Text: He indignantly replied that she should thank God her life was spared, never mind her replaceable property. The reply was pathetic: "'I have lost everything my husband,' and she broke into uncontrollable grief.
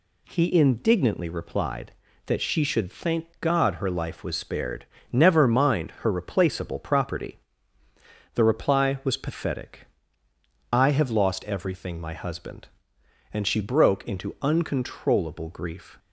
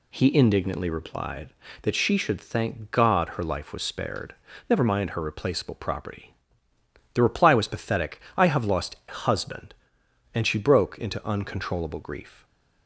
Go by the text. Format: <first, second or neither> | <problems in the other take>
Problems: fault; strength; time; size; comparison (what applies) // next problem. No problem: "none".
first | skips "everything my"; at 9.0 s